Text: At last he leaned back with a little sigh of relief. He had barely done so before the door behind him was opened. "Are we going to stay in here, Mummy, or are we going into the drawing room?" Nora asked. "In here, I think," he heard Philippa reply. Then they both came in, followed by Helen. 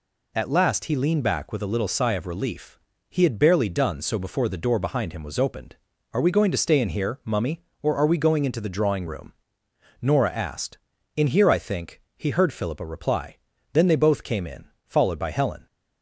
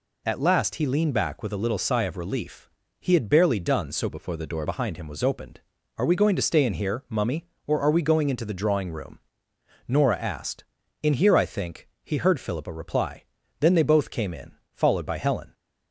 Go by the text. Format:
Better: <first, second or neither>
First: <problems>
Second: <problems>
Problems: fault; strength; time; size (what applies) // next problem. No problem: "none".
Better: first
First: none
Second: changes voice from "before" to "door"; from 4.0 to 4.6 s; 0.6 s long